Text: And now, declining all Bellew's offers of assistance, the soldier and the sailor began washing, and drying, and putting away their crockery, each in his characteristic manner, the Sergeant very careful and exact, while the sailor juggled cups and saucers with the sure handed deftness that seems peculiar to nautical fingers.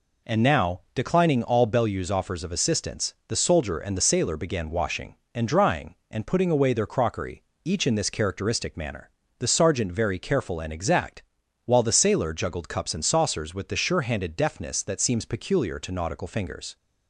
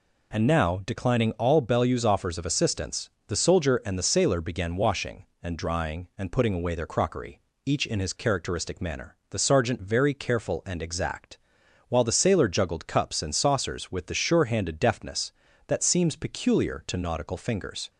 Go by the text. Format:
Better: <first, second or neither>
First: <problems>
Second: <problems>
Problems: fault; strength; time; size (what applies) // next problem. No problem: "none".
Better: second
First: says "this" for "his"; at 7.9 s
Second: none